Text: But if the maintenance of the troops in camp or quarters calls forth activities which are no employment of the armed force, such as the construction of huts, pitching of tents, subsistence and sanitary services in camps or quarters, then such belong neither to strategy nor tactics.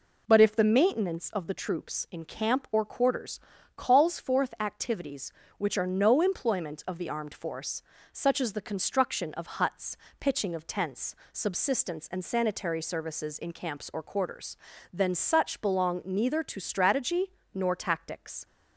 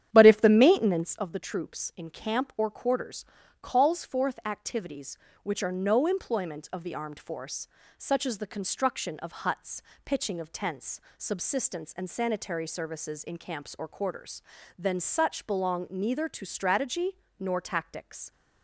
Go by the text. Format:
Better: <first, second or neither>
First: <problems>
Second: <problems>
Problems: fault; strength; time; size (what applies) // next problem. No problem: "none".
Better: first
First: pauses between "quarters" and "calls"; slight; at 3.3 s; 0.36 s long // pauses between "strategy" and "nor"; slight; at 17.3 s; 0.22 s long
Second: starts louder than the rest; strong; until 1.3 s; 10 dB // pauses between "quarters" and "calls"; slight; at 3.2 s; 0.36 s long // pauses between "strategy" and "nor"; slight; at 17.1 s; 0.22 s long